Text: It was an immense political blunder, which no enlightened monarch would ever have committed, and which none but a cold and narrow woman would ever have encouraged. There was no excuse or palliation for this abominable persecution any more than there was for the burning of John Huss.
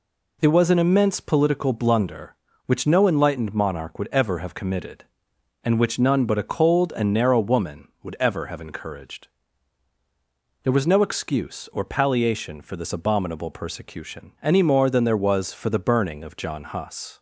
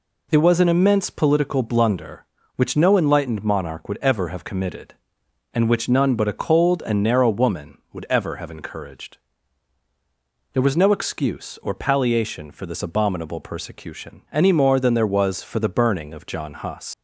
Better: first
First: none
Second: leaves "Huss" unfinished; at 16.9 s; 155 ms

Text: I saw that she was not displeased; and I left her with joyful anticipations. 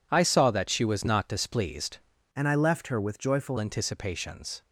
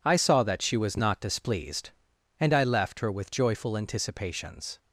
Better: second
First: changes voice from "and" to "joyful"; from 2.3 to 3.5 s; 1.2 s long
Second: none

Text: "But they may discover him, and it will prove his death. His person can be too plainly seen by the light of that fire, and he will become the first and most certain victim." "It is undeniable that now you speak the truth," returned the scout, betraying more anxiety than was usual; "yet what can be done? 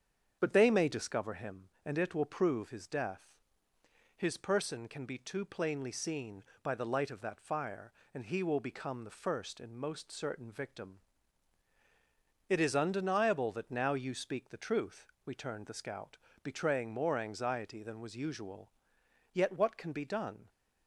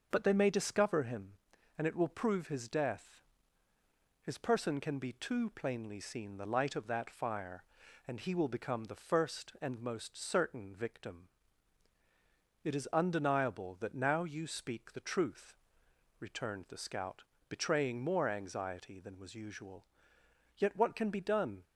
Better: first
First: starts louder than the rest; strong; until 1.4 s; 7.5 dB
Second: starts louder than the rest; until 1.1 s; 6.5 dB // skips "by"; at 6.3 s

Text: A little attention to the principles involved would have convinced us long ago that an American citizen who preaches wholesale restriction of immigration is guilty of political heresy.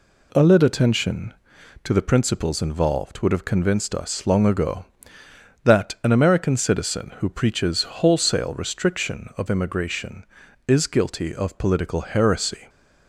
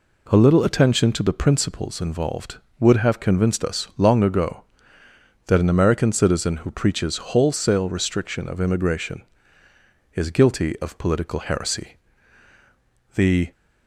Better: first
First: none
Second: goes on to say "The"; slight; from 13.1 s on; 0.36 s long

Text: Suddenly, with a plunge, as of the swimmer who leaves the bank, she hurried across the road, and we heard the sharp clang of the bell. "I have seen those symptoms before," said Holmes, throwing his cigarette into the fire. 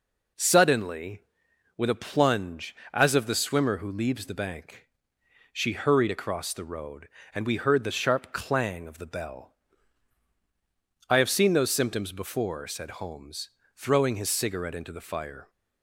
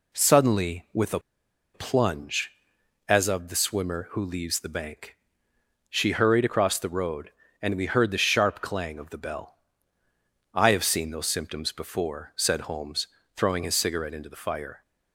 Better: first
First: none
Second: pauses between "a" and "plunge"; noticeable; at 1.1 s; 0.54 s long

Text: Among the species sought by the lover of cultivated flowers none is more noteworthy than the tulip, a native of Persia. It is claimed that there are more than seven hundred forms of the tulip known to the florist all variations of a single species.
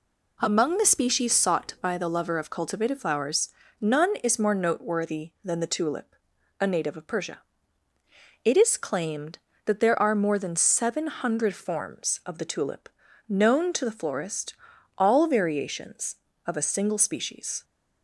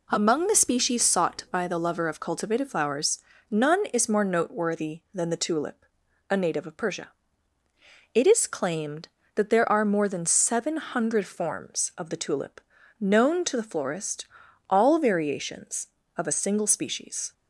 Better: neither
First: pauses between "flowers" and "none"; slight; at 3.4 s; 0.32 s long // pauses between "tulip" and "known"; at 12.9 s; 0.40 s long // pauses between "florist" and "all"; at 14.5 s; 0.44 s long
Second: pauses between "flowers" and "none"; slight; at 3.1 s; 0.32 s long // pauses between "tulip" and "known"; at 12.6 s; 0.40 s long // pauses between "florist" and "all"; at 14.2 s; 0.44 s long

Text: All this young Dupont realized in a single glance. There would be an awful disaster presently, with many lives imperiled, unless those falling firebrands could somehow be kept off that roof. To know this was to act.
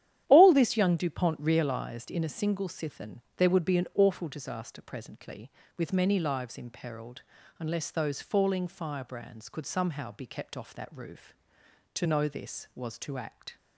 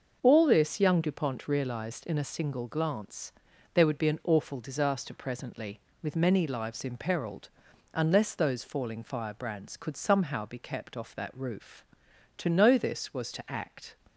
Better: second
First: starts louder than the rest; strong; until 1.2 s; 11 dB // says "sithen" for "glance"; at 2.6 s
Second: starts louder than the rest; noticeable; until 1.2 s; 6 dB

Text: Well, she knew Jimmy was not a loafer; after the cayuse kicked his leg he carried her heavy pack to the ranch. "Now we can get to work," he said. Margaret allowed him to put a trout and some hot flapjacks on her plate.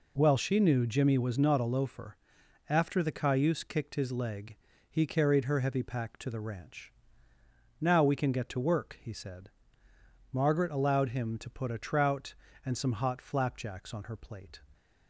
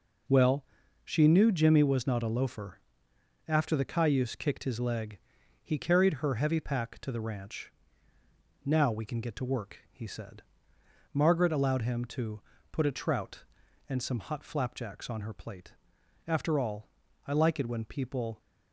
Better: first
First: pauses between "leg" and "he"; slight; at 4.5 s; 0.32 s long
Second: pauses between "leg" and "he"; at 5.1 s; 0.44 s long // pauses between "to" and "put"; slight; at 12.4 s; 0.32 s long // goes on to say "After all I like it when people"; strong; from 16.2 s on; 2.1 s long

